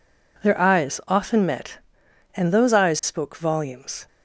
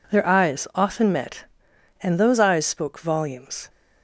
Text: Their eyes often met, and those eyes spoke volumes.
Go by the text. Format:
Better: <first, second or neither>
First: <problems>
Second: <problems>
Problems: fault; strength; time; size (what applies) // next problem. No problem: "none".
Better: neither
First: none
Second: none